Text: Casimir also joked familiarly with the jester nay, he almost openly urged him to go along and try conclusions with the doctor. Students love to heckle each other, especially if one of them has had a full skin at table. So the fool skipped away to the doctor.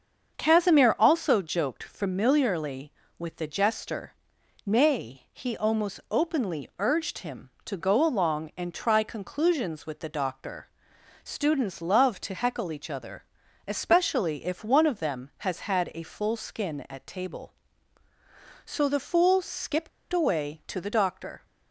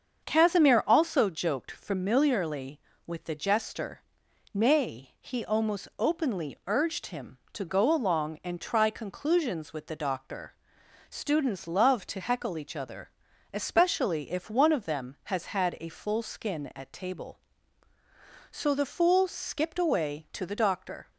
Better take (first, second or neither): second